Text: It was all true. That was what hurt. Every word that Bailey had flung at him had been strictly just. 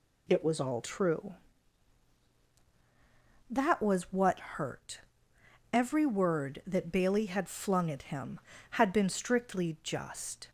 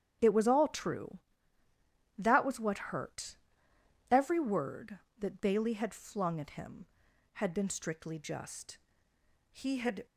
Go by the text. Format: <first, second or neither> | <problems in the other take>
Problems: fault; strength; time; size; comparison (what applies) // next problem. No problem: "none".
first | starts louder than the rest; strong; until 2.2 s; 9 dB // goes on to say "He had"; from 9.5 s on; 0.54 s long